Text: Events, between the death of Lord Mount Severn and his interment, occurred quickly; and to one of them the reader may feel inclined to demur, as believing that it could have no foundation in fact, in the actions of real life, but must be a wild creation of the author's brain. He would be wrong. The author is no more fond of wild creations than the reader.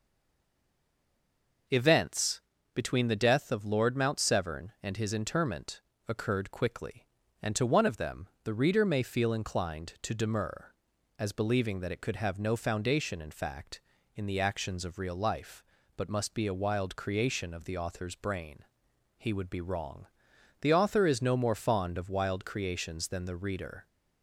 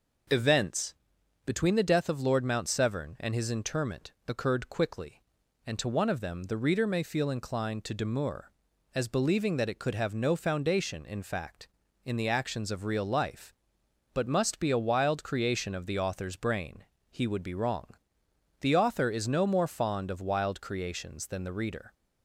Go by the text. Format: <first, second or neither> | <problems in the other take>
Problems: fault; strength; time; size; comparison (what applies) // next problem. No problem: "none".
second | stays silent before the first word; noticeable; until 1.6 s; 1.6 s long // pauses between "them" and "the"; slight; at 8.2 s; 0.16 s long